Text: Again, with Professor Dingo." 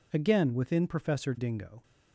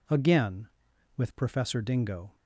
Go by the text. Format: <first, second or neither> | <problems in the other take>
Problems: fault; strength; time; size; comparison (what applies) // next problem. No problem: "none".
second | says "within" for "with"; at 0.5 s